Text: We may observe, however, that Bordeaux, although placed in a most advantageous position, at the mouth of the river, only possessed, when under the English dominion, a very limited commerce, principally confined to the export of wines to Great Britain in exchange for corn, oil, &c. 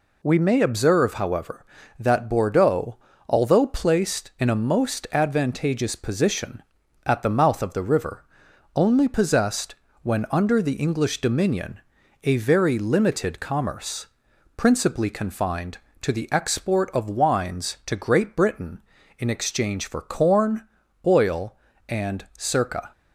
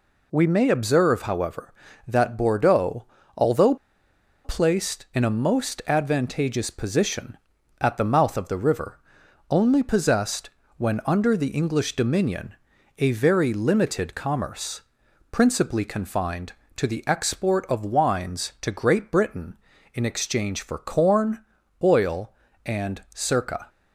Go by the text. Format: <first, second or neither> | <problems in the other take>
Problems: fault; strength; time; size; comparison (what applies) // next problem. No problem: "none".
first | pauses between "although" and "placed"; noticeable; at 3.7 s; 0.69 s long